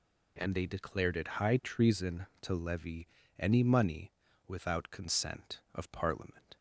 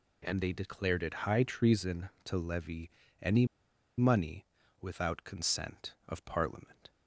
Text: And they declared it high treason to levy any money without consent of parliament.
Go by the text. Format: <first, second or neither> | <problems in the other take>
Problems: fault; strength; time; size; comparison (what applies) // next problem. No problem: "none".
first | pauses between "levy" and "any"; slight; at 2.8 s; 0.32 s long; slight in the first // pauses between "any" and "money"; noticeable; at 3.4 s; 0.52 s long // pauses between "money" and "without"; at 4.4 s; 0.38 s long; also in the first